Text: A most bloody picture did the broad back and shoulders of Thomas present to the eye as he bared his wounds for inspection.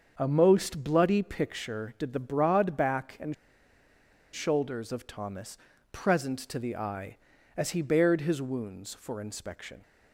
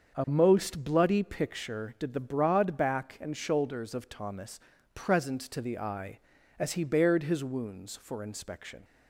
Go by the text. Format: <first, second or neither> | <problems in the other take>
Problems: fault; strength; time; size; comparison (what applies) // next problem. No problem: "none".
second | starts louder than the rest; until 1.1 s; 7 dB; also in the second // pauses between "and" and "shoulders"; at 3.3 s; 0.99 s long // pauses between "Thomas" and "present"; slight; at 5.5 s; 0.34 s long; slight in the second